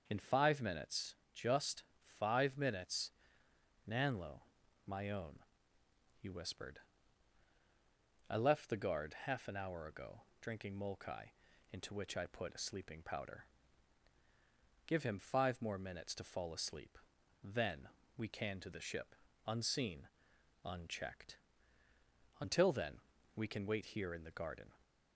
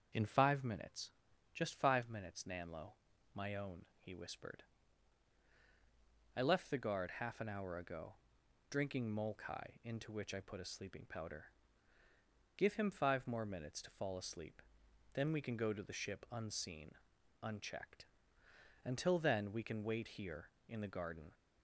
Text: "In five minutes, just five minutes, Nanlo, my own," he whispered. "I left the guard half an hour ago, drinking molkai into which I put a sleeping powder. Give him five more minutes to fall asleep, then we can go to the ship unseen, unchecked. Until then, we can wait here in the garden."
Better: second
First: starts louder than the rest; until 1.0 s; 6.5 dB // pauses between "just" and "five"; slight; at 1.8 s; 0.36 s long // pauses between "molkai" and "into"; at 11.2 s; 0.42 s long // pauses between "then" and "we"; slight; at 17.8 s; 0.26 s long // skips "go"; at 18.5 s // pauses between "ship" and "unseen"; slight; at 19.1 s; 0.32 s long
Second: starts louder than the rest; until 1.5 s; 7 dB

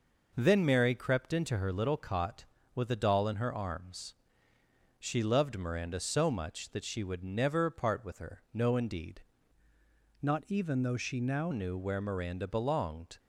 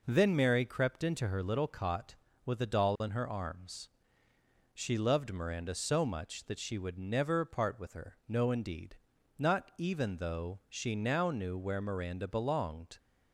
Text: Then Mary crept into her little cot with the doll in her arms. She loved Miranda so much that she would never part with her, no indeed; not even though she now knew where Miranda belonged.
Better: second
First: changes voice from "not" to "now"; from 10.2 to 11.5 s; 1.3 s long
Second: none

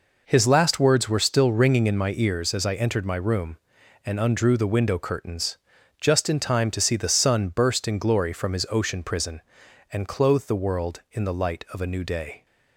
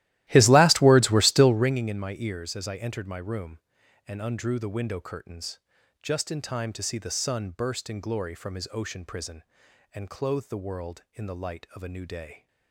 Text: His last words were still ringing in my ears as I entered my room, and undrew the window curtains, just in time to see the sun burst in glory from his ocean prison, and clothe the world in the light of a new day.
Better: first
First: none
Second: starts louder than the rest; strong; until 1.8 s; 15.5 dB

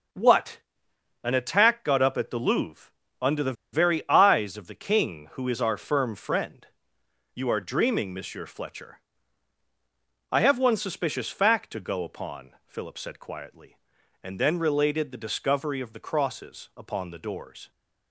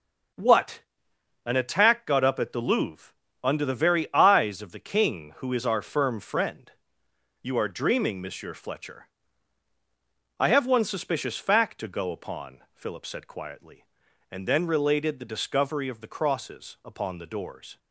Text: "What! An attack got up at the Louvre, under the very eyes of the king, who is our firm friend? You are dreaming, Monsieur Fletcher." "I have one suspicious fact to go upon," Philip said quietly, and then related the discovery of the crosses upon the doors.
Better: second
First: starts louder than the rest; until 1.7 s; 6.5 dB // pauses between "the" and "very"; slight; at 3.5 s; 0.19 s long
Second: starts louder than the rest; until 1.9 s; 6.5 dB

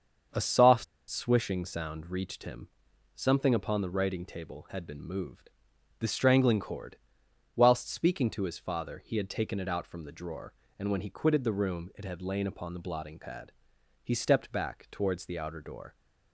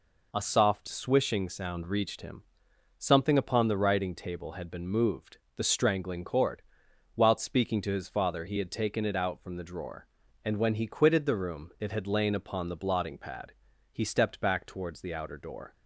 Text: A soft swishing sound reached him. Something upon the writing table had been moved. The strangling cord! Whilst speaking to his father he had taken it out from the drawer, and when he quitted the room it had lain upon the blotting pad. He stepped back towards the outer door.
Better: second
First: starts louder than the rest; until 1.5 s; 6.5 dB // pauses between "soft" and "swishing"; slight; at 0.8 s; 0.23 s long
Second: none

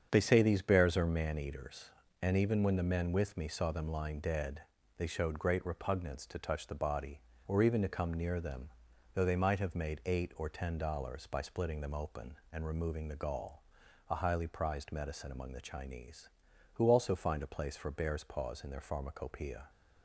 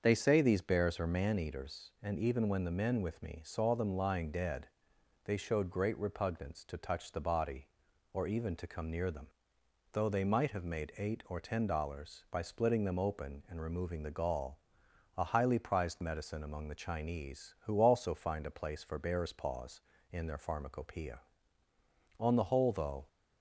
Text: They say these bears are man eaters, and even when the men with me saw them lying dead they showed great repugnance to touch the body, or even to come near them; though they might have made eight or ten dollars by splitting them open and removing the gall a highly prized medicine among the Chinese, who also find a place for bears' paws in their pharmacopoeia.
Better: first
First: starts louder than the rest; strong; until 1.1 s; 7.5 dB // pauses between "dead" and "they"; slight; at 4.6 s; 0.36 s long // pauses between "gall" and "a"; noticeable; at 13.6 s; 0.48 s long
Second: starts louder than the rest; until 1.0 s; 6.5 dB // pauses between "dead" and "they"; noticeable; at 4.6 s; 0.58 s long // pauses between "gall" and "a"; noticeable; at 14.5 s; 0.58 s long // goes on to say "On the whole though"; noticeable; from 22.1 s on; 0.88 s long

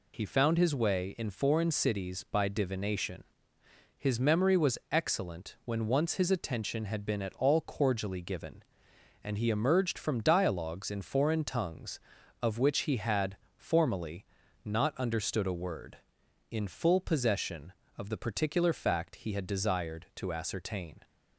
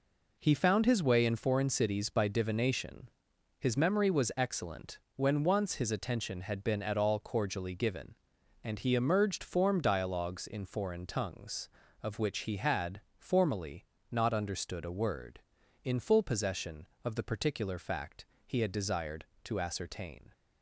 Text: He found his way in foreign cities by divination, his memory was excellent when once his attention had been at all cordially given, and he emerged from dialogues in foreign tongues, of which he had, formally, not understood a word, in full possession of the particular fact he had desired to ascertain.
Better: first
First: none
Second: pauses between "excellent" and "when"; slight; at 5.0 s; 0.16 s long // says "form" for "from"; at 9.4 s // pauses between "fact" and "he"; slight; at 18.2 s; 0.22 s long

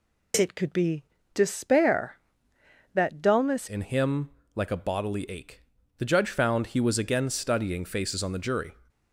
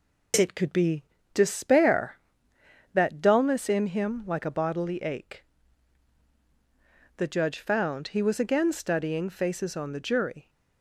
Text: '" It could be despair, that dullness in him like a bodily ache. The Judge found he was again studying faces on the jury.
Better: second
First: pauses between "be" and "despair"; slight; at 1.0 s; 0.28 s long // changes voice at "in"; from 3.6 s on; 5.1 s long // pauses between "him" and "like"; slight; at 4.2 s; 0.24 s long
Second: pauses between "be" and "despair"; slight; at 1.0 s; 0.28 s long

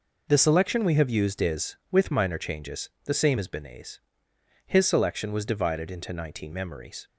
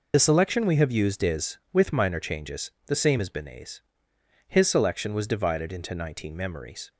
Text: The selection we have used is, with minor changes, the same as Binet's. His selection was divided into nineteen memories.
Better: first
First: none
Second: loses the start of "The"; at 0.1 s; 40 ms

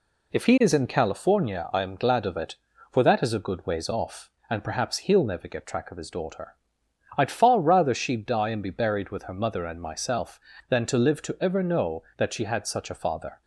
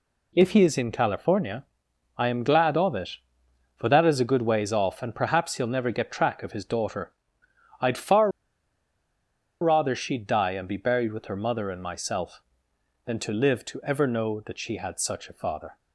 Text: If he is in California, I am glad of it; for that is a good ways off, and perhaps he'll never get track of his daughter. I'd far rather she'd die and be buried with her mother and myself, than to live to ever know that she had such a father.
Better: first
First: none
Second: pauses between "far" and "rather"; strong; at 8.3 s; 1.3 s long

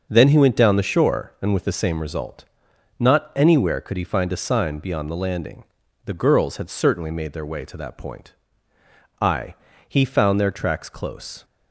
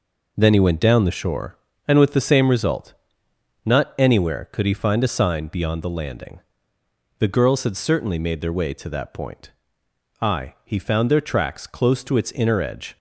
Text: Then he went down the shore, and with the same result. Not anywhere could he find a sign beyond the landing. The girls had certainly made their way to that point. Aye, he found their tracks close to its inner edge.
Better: second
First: starts louder than the rest; until 1.1 s; 6 dB // stops before "to its inner edge"; at 11.4 s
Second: none

